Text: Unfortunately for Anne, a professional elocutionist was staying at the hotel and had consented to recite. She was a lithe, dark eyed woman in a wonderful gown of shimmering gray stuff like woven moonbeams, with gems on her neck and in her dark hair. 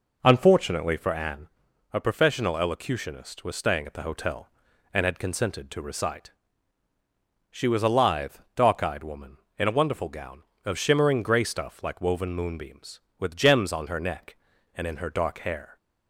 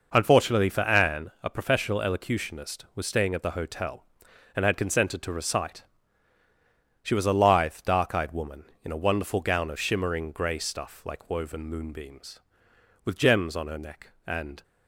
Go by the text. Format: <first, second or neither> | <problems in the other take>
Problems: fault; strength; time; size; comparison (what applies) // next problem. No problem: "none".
first | stops before "in her dark hair"; at 14.6 s